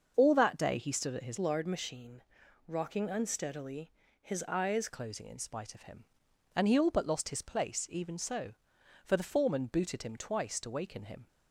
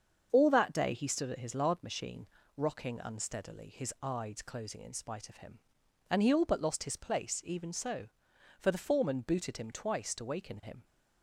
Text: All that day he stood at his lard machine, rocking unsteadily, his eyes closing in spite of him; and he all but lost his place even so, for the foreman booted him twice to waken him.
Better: second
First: starts louder than the rest; until 1.1 s; 6.5 dB // changes voice from "lard" to "eyes"; from 1.3 to 4.8 s; 3.5 s long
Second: starts louder than the rest; until 1.3 s; 7 dB

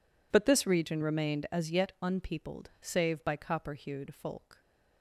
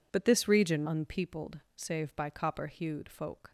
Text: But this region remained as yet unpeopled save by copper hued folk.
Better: first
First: none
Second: skips "remained as yet"; at 0.8 s // pauses between "unpeopled" and "save"; slight; at 1.5 s; 0.16 s long

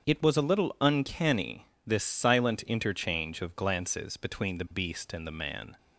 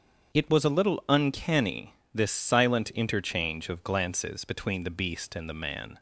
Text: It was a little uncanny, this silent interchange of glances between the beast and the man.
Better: neither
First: starts louder than the rest; until 1.1 s; 7 dB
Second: starts louder than the rest; until 1.4 s; 7 dB

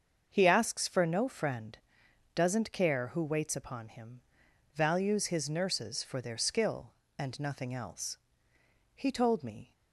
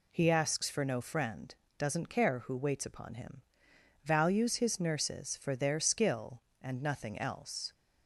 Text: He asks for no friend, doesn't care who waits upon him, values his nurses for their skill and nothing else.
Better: second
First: starts louder than the rest; until 1.3 s; 6.5 dB // goes on to say "He told me"; noticeable; from 8.9 s on; 0.78 s long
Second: none

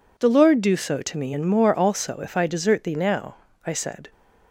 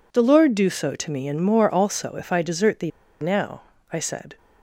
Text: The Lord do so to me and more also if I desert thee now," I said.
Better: first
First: none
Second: pauses between "thee" and "now"; slight; at 2.9 s; 0.30 s long

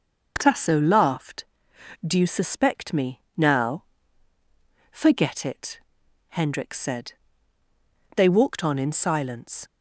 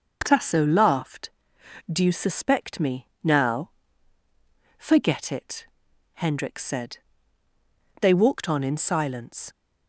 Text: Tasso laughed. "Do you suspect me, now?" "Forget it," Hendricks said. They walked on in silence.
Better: neither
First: starts louder than the rest; noticeable; until 1.3 s; 6 dB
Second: starts louder than the rest; noticeable; until 1.2 s; 6 dB

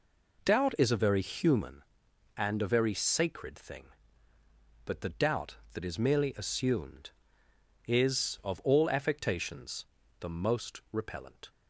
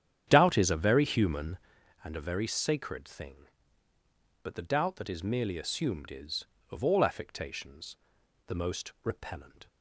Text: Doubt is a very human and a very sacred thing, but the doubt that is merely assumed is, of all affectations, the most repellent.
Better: first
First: none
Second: starts louder than the rest; strong; until 1.7 s; 9.5 dB

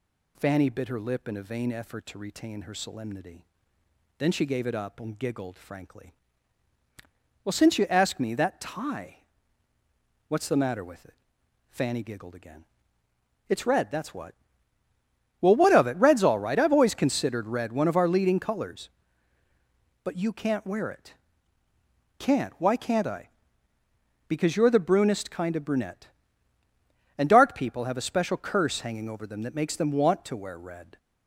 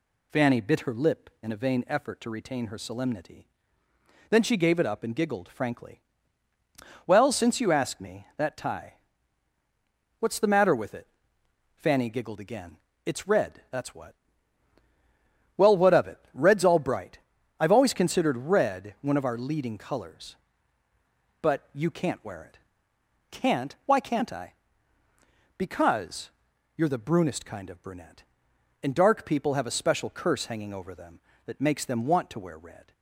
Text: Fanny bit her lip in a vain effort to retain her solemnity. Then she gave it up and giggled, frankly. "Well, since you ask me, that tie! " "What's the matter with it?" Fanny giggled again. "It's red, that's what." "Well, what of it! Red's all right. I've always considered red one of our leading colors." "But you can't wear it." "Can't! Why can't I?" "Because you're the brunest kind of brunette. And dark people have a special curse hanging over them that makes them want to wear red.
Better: first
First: none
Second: says "bright" for "right"; at 16.7 s // pauses between "Because" and "you're"; noticeable; at 26.2 s; 0.46 s long

